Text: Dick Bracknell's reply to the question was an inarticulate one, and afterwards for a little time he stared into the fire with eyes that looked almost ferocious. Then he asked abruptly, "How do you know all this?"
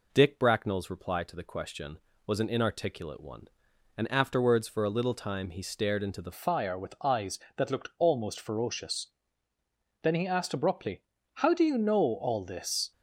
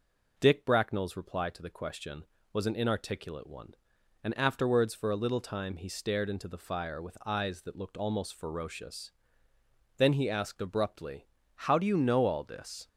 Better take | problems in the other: second | changes voice at "fire"; from 6.3 s on; 6.6 s long

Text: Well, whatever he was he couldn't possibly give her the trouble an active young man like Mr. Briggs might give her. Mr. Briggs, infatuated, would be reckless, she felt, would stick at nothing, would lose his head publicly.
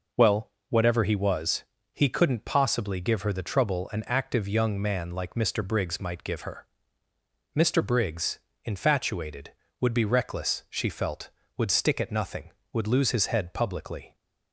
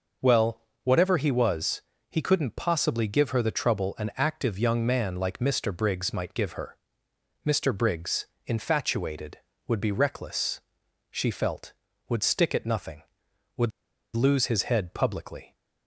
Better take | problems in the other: first | pauses between "was" and "he"; slight; at 1.8 s; 0.26 s long; slight in the first // pauses between "would" and "lose"; noticeable; at 13.7 s; 0.46 s long

